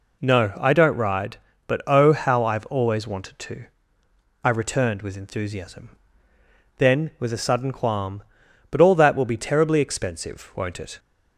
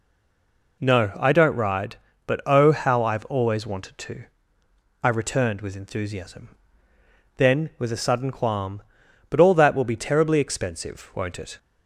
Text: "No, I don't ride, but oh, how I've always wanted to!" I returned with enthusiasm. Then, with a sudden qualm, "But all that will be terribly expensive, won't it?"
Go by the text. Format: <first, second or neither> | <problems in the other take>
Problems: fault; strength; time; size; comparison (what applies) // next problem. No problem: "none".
first | stays silent before the first word; slight; until 0.7 s; 0.7 s long